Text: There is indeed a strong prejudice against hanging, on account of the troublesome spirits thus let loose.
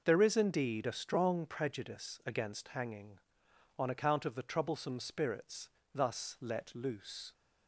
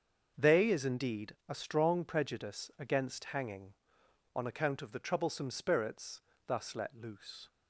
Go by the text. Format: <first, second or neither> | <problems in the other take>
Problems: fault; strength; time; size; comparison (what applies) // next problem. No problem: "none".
first | starts louder than the rest; until 1.3 s; 6.5 dB // says "They" for "There"; at 0.3 s // pauses between "spirits" and "thus"; slight; at 6.2 s; 0.26 s long; slight in the first